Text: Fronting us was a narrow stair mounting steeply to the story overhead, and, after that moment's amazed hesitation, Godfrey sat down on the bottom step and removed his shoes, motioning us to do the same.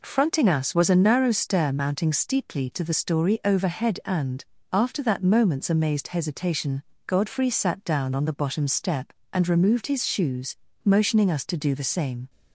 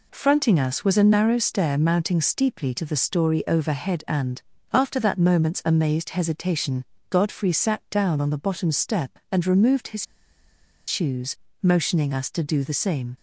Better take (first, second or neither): first